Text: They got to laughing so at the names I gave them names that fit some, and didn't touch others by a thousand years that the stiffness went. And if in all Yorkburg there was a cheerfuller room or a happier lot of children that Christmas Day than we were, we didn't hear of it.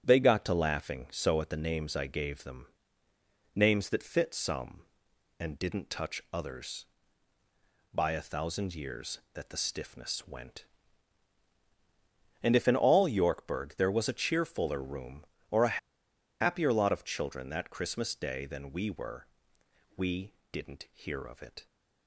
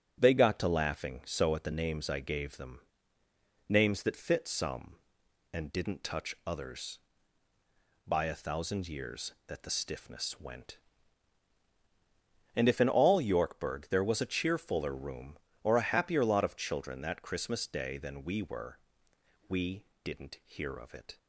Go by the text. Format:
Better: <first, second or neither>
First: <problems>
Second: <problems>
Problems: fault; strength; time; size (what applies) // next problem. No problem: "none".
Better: second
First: starts louder than the rest; strong; until 1.0 s; 8 dB // pauses between "them" and "names"; noticeable; at 2.6 s; 0.90 s long // pauses between "a" and "happier"; noticeable; at 15.7 s; 0.61 s long // pauses between "we" and "didn't"; slight; at 20.3 s; 0.22 s long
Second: starts louder than the rest; strong; until 1.2 s; 7.5 dB // pauses between "them" and "names"; noticeable; at 2.8 s; 0.90 s long // pauses between "we" and "didn't"; slight; at 19.8 s; 0.22 s long